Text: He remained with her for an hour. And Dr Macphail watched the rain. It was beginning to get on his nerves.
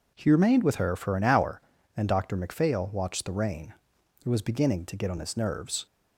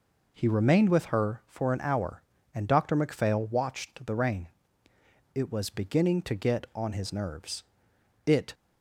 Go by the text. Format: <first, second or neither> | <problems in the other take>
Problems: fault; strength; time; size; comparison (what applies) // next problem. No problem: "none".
first | goes on to say "It"; slight; from 8.2 s on; 0.28 s long